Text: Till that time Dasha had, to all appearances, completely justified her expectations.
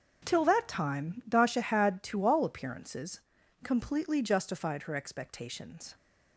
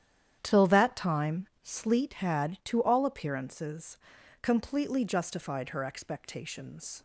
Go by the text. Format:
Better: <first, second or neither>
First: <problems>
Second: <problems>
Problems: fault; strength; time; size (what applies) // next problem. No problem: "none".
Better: first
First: starts louder than the rest; until 1.3 s; 6.5 dB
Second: starts louder than the rest; strong; until 1.4 s; 10 dB // says "Sleet" for "Dasha"; at 1.6 s